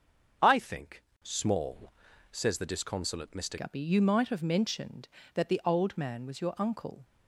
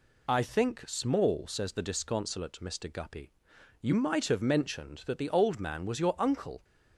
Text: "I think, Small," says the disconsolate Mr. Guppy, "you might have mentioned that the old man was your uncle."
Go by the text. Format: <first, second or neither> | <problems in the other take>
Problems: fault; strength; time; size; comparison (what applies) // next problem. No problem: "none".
second | starts louder than the rest; until 1.6 s; 6.5 dB // changes voice at "Guppy"; from 3.5 s on; 3.5 s long